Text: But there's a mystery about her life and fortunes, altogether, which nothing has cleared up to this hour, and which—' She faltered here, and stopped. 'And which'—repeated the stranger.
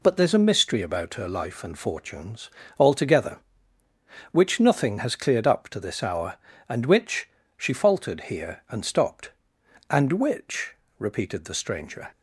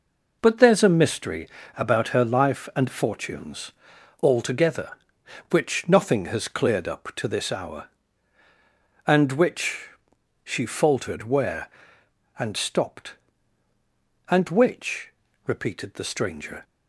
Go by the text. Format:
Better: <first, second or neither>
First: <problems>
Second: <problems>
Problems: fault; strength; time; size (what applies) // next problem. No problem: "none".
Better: first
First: none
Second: pauses between "mystery" and "about"; slight; at 1.4 s; 0.28 s long // says "where" for "here"; at 11.2 s